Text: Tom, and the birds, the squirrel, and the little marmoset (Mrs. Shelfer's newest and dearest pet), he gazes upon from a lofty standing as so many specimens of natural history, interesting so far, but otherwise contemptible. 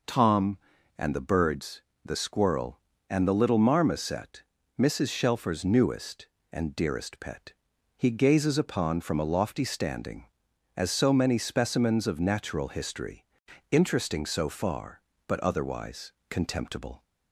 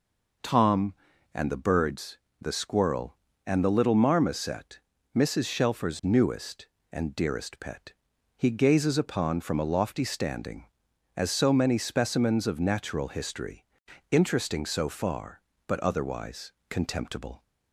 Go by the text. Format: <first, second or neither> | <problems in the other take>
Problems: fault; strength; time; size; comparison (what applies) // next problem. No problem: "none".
neither | pauses between "otherwise" and "contemptible"; slight; the same in both